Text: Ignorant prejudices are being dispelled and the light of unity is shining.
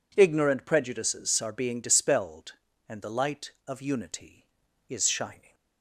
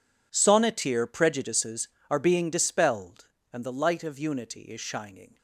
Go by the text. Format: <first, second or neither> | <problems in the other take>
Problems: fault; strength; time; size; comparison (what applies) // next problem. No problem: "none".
first | says "Sonneteer" for "Ignorant"; at 0.3 s